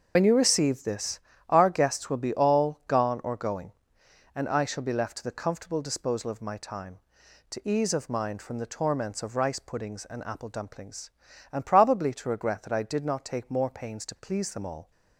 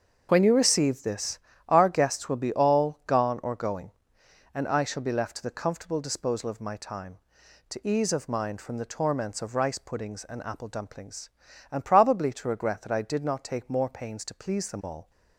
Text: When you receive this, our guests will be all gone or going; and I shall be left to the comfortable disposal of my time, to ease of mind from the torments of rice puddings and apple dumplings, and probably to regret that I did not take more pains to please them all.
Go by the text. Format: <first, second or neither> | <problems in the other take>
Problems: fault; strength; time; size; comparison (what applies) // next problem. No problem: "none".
second | loses the start of "When"; at 0.1 s; 55 ms // starts louder than the rest; until 1.1 s; 6.5 dB; also in the second